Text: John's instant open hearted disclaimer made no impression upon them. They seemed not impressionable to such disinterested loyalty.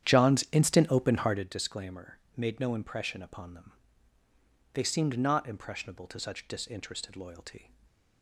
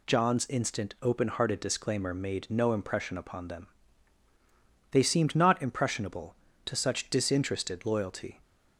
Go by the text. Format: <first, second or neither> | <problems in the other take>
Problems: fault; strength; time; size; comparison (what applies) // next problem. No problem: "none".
second | starts louder than the rest; strong; until 1.5 s; 10 dB // pauses between "disclaimer" and "made"; slight; at 2.1 s; 0.18 s long // stays silent after the last word; slight; from 7.6 s on; 0.6 s long